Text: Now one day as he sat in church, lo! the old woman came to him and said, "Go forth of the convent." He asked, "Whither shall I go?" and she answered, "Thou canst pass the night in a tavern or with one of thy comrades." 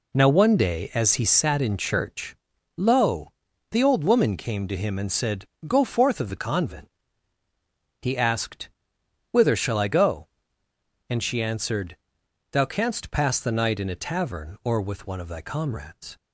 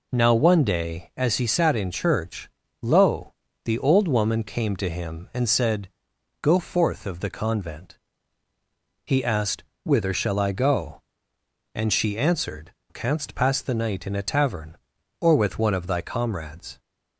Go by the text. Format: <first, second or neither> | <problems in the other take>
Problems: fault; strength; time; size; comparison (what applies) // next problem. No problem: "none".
first | skips "Thou"; at 12.8 s